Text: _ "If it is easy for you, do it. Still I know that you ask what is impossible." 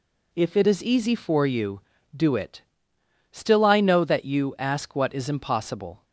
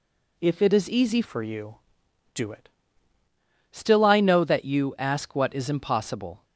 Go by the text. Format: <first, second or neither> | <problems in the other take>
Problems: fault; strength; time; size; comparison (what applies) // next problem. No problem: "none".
first | changes voice from "for" to "it"; from 1.2 to 2.6 s; 1.4 s long